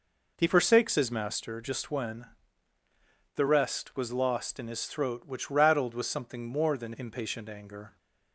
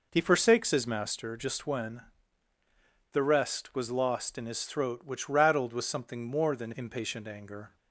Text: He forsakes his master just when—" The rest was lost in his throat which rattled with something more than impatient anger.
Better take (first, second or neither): neither